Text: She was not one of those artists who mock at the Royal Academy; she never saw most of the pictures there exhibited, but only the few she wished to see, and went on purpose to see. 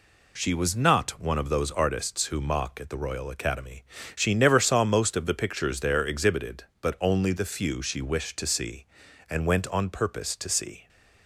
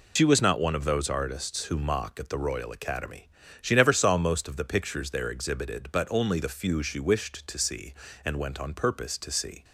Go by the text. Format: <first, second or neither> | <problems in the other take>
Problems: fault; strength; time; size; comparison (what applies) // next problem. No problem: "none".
first | loses the start of "She"; at 0.1 s; 75 ms